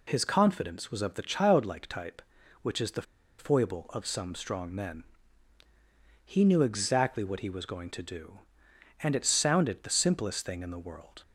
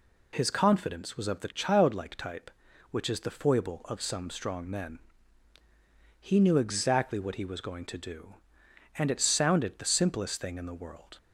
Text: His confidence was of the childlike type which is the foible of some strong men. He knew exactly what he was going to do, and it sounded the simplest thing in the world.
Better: second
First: pauses between "the" and "foible"; at 3.0 s; 0.36 s long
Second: none

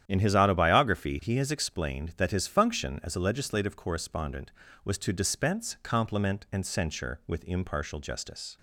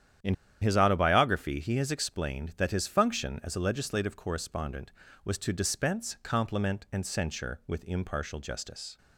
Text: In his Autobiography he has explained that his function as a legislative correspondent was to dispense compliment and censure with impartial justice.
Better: first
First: starts louder than the rest; strong; until 1.0 s; 10 dB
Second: starts louder than the rest; strong; until 1.5 s; 10 dB // pauses between "In" and "his"; slight; at 0.3 s; 0.27 s long

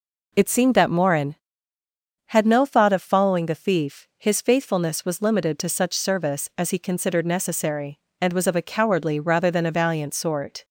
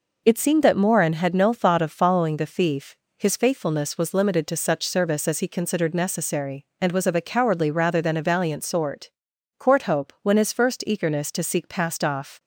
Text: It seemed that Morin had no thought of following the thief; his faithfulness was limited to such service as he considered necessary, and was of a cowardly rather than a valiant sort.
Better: first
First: none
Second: goes on to say "Courthope when his first eagerness to seek passed off"; strong; from 9.5 s on; 2.8 s long

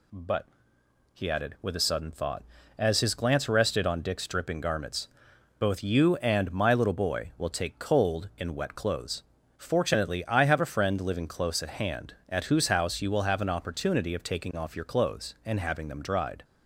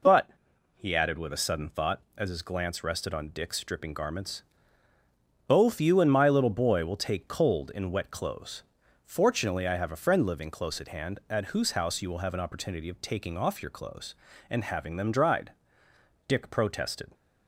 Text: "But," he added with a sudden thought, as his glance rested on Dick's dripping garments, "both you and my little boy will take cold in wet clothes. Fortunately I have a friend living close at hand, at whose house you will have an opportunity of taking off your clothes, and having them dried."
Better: first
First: none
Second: goes on to say "Dick protested"; noticeable; from 16.2 s on; 0.82 s long

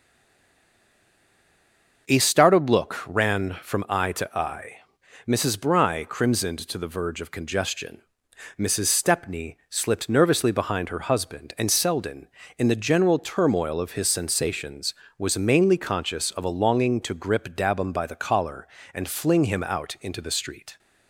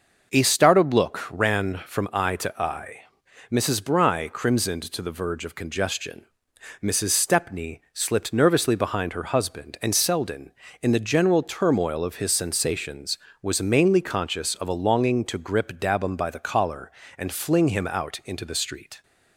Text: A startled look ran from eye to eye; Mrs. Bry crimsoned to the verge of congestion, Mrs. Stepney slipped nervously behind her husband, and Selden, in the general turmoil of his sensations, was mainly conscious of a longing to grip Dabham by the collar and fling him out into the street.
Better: second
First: stays silent before the first word; noticeable; until 2.0 s; 2.0 s long // starts louder than the rest; noticeable; until 3.1 s; 6 dB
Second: starts louder than the rest; until 1.4 s; 6 dB

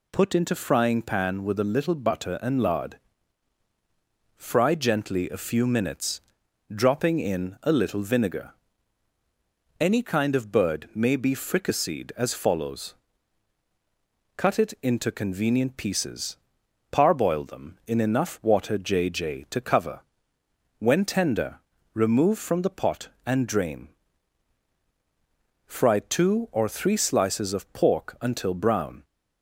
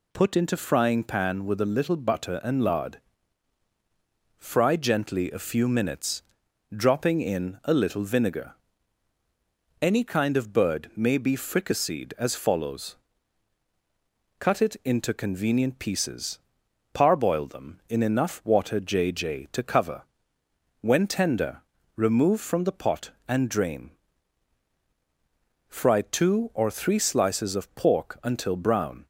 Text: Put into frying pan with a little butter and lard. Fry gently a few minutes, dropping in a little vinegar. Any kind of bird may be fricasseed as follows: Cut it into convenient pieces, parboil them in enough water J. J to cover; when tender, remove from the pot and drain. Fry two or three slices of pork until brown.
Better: neither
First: none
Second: none

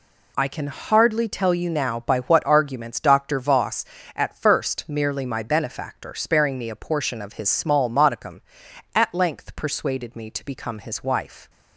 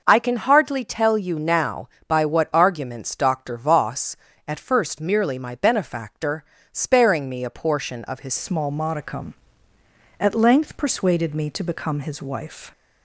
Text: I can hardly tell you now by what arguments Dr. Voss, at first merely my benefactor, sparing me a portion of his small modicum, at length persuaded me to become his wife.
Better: first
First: none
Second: changes voice at "small"; from 8.3 s on; 4.4 s long

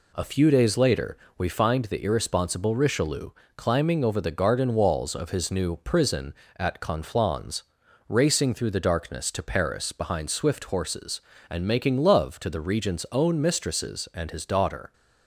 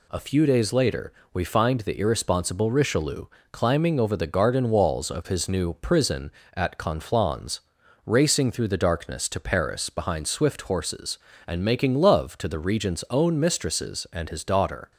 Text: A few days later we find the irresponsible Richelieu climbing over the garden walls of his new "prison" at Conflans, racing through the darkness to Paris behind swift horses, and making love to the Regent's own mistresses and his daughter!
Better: second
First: starts louder than the rest; slight; until 1.6 s; 2.5 dB // pauses between "later" and "we"; slight; at 1.1 s; 0.22 s long // pauses between "Richelieu" and "climbing"; slight; at 3.2 s; 0.26 s long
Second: pauses between "later" and "we"; slight; at 1.1 s; 0.22 s long // pauses between "Richelieu" and "climbing"; slight; at 3.2 s; 0.26 s long

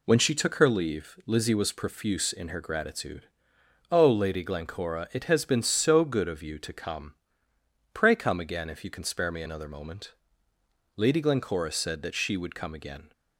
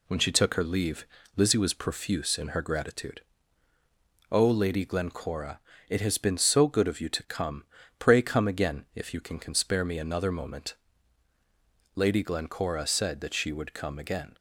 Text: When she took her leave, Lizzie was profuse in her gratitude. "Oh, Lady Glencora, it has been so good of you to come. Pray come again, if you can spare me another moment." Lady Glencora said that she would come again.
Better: first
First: none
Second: says "can" twice; at 9.3 s

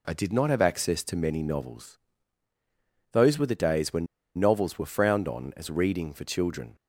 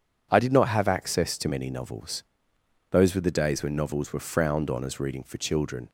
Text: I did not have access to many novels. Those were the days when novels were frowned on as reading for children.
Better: second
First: pauses between "when" and "novels"; slight; at 4.0 s; 0.30 s long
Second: none

